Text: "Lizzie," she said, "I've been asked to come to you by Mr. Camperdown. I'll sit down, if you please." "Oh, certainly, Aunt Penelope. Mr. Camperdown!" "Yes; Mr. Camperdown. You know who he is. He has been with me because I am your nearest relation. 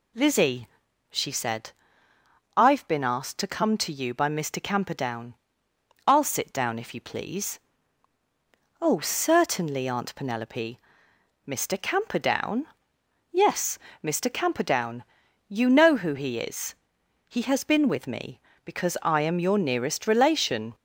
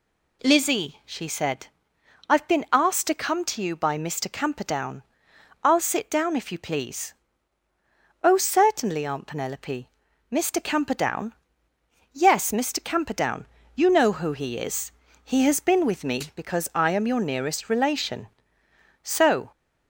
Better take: first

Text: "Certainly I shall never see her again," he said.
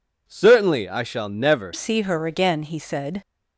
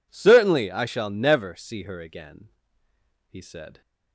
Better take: second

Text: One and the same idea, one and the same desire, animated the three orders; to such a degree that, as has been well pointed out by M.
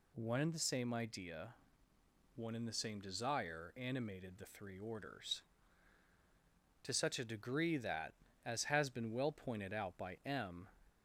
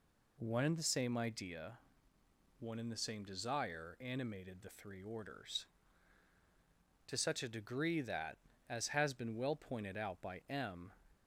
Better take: first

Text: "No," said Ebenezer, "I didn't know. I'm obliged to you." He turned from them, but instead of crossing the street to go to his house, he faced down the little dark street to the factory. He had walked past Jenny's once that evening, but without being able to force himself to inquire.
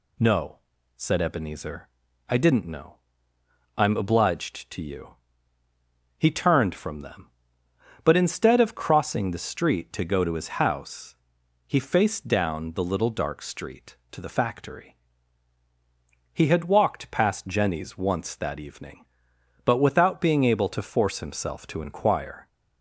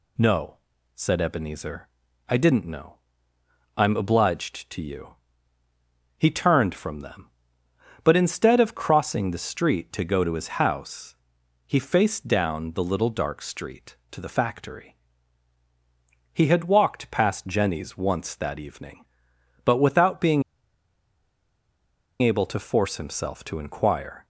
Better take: first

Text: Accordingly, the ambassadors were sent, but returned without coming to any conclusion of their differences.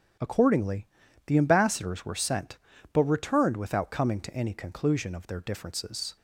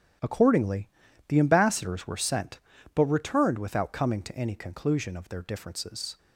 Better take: first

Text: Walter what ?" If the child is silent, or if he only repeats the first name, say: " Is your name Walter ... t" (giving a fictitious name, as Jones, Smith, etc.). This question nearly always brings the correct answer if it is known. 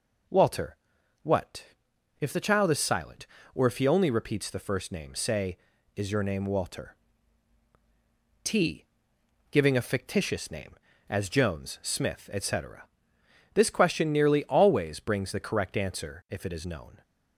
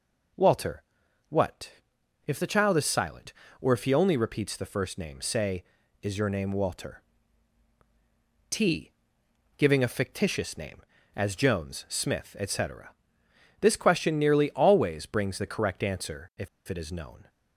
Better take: first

